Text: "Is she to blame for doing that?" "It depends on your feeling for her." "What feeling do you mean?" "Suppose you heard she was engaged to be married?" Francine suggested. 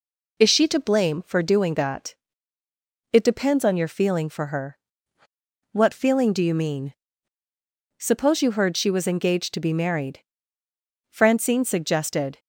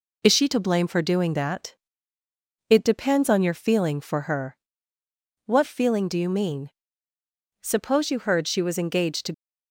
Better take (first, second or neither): first